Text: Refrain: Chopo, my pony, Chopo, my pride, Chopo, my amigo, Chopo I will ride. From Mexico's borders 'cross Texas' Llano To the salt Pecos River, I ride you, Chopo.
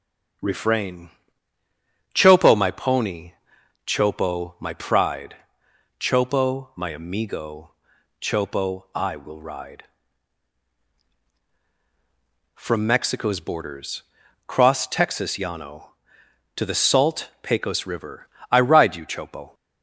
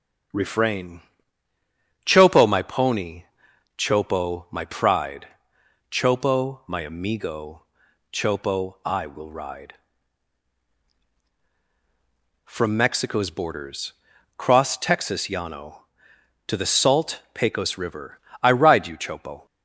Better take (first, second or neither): neither